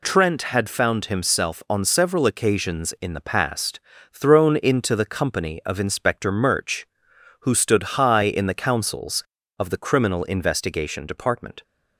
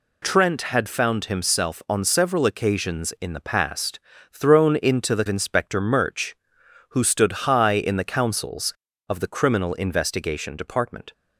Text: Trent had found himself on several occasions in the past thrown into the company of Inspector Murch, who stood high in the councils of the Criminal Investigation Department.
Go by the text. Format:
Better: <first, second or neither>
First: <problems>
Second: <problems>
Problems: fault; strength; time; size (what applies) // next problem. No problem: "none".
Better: first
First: pauses between "past" and "thrown"; slight; at 3.7 s; 0.32 s long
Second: pauses between "past" and "thrown"; slight; at 3.9 s; 0.32 s long // skips "company of"; at 5.2 s